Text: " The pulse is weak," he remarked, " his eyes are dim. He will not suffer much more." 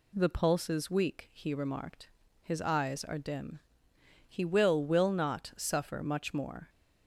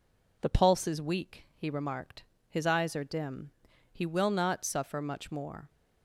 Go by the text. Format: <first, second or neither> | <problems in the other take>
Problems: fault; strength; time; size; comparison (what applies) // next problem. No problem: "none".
second | says "will" twice; at 4.8 s